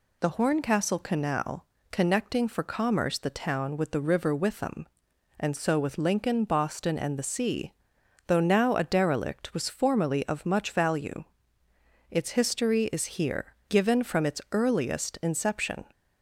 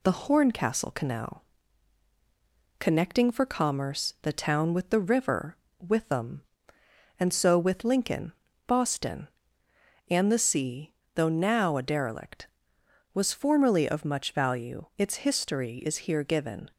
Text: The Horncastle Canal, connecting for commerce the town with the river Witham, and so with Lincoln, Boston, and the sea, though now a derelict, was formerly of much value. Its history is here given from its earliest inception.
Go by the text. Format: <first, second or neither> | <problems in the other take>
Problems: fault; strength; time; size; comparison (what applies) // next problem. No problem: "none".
first | pauses between "river" and "Witham"; slight; at 5.5 s; 0.22 s long // stops before "from its earliest inception"; at 16.7 s